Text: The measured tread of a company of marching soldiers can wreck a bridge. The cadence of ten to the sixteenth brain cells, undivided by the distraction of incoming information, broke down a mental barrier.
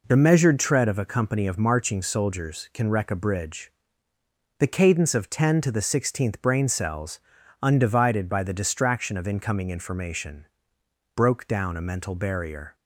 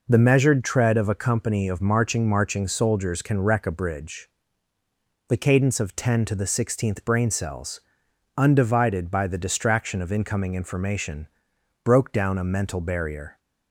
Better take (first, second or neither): first